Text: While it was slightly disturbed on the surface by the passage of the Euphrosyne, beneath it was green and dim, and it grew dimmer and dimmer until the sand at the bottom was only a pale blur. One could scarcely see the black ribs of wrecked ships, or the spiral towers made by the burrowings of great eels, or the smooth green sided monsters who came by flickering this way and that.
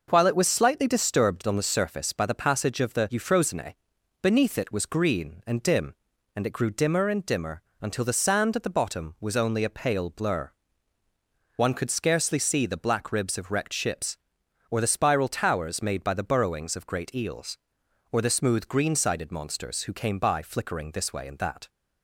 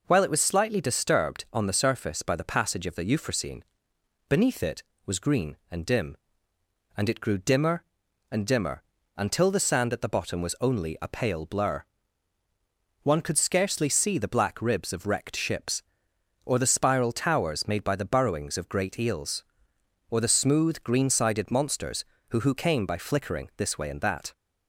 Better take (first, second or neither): first